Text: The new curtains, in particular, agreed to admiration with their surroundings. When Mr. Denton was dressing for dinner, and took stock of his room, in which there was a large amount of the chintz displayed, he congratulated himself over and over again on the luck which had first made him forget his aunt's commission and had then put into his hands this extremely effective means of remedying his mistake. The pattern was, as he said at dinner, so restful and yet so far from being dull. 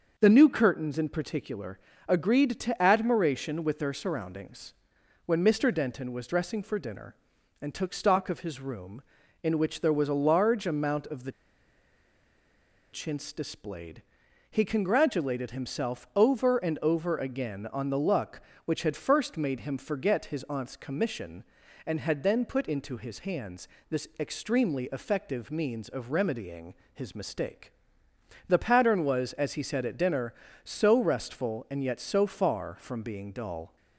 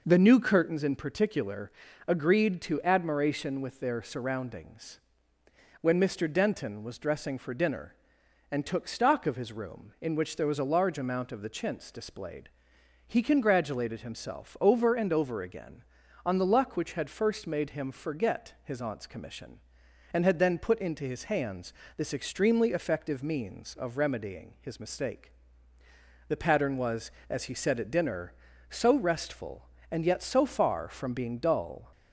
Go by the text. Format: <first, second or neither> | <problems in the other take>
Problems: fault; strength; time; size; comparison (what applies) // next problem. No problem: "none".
second | starts louder than the rest; until 1.2 s; 6 dB // pauses between "the" and "chintz"; strong; at 11.3 s; 1.6 s long // pauses between "hands" and "this"; slight; at 23.6 s; 0.22 s long; slight in the second // pauses between "remedying" and "his"; slight; at 26.7 s; 0.20 s long